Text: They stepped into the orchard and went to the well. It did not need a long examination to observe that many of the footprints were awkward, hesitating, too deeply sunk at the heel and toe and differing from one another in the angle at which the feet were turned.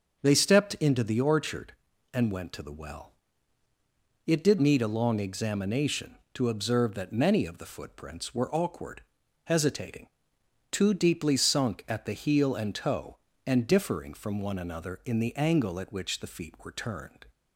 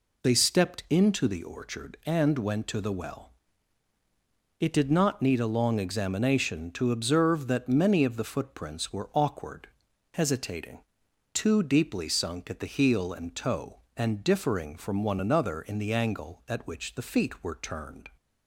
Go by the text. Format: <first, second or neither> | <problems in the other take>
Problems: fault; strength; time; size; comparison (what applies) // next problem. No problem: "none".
second | starts louder than the rest; until 1.2 s; 6.5 dB // skips "not"; at 4.5 s